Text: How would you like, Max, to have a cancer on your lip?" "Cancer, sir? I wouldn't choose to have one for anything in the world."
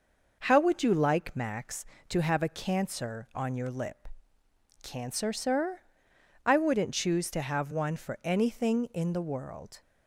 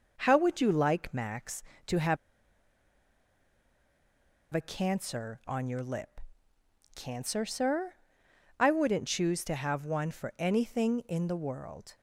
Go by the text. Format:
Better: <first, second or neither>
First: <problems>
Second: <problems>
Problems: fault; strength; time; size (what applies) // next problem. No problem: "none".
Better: first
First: none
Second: pauses between "have" and "a"; strong; at 2.1 s; 2.3 s long